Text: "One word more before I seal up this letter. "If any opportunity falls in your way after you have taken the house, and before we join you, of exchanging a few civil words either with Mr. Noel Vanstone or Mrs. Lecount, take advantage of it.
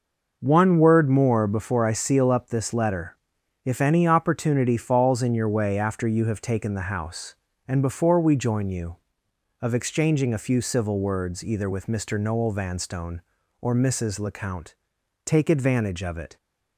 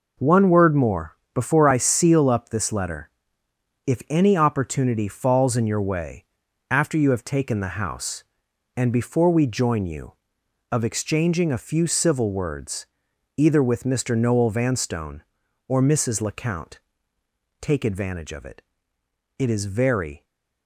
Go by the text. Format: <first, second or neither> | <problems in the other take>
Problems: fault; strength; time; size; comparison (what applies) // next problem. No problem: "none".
first | pauses between "more" and "before"; slight; at 1.1 s; 0.16 s long // pauses between "way" and "after"; noticeable; at 6.2 s; 0.46 s long // pauses between "words" and "either"; noticeable; at 12.8 s; 0.48 s long // goes on to say "It is very"; noticeable; from 19.3 s on; 0.86 s long